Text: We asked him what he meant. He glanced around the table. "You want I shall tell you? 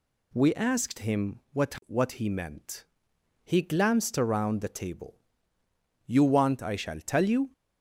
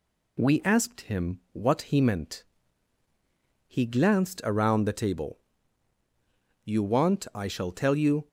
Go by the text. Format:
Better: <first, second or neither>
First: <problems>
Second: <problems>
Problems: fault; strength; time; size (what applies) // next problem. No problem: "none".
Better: second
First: says "what" twice; at 1.8 s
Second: none